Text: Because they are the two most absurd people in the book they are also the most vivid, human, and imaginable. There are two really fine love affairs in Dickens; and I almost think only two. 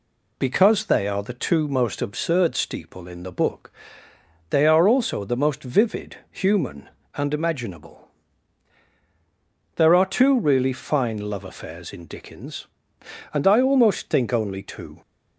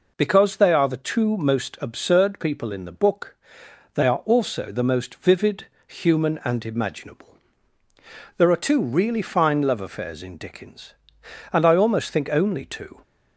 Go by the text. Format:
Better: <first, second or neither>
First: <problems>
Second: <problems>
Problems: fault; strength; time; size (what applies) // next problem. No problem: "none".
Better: second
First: says "steeple" for "people"; at 2.5 s // pauses between "book" and "they"; noticeable; at 3.7 s; 0.78 s long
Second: pauses between "book" and "they"; noticeable; at 3.3 s; 0.60 s long